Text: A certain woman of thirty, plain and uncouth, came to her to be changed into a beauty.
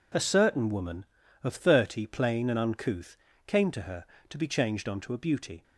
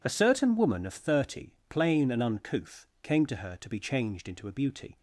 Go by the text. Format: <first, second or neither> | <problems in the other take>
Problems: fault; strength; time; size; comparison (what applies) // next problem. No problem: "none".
second | says "onto" for "into"; at 4.8 s